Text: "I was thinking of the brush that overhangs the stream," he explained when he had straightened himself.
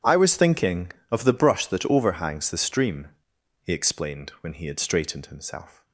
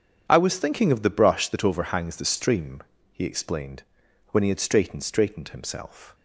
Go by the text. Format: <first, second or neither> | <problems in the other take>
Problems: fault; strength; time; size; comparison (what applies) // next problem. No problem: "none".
first | starts louder than the rest; strong; until 1.2 s; 8 dB // pauses between "explained" and "when"; noticeable; at 3.8 s; 0.46 s long // says "straightened" twice; at 5.0 s